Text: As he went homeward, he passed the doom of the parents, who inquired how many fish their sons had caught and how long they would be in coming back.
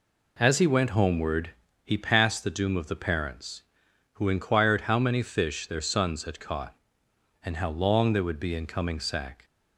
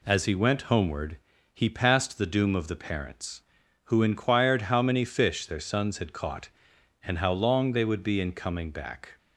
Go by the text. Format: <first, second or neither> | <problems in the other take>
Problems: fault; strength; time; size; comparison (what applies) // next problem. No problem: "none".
second | says "sack" for "back"; at 9.0 s